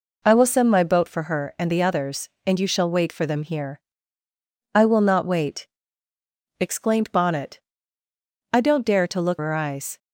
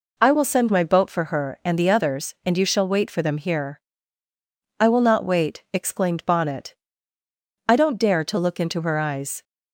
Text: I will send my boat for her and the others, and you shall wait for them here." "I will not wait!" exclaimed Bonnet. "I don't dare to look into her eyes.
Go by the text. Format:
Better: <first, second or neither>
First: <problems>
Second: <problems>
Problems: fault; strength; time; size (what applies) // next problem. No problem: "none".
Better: second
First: skips "into"; at 9.3 s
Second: none